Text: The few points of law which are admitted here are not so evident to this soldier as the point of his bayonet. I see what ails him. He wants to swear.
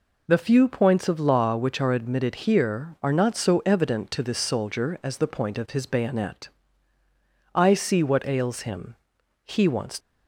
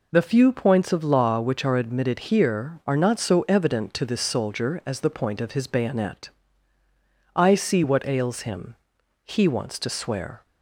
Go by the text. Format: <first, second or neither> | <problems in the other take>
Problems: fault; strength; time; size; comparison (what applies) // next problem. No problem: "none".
second | stops before "to swear"; at 9.9 s